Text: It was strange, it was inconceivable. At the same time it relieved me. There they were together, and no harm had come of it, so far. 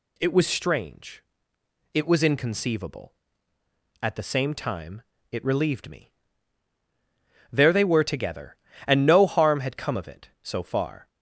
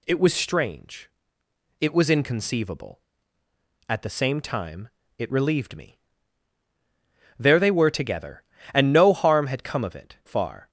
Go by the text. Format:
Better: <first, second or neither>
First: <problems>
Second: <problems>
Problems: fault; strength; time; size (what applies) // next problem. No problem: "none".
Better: first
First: pauses between "time" and "it"; slight; at 5.0 s; 0.28 s long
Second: pauses between "time" and "it"; slight; at 4.8 s; 0.28 s long // skips "so"; at 10.2 s